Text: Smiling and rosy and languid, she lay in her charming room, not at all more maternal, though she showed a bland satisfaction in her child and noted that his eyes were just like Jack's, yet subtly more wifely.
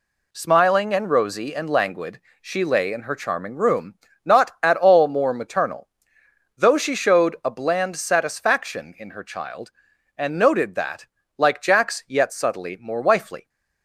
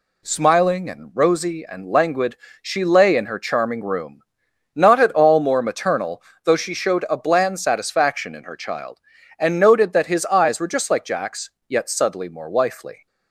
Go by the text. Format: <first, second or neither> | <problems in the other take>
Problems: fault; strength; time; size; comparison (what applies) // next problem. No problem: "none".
second | skips "his eyes were just"; at 11.2 s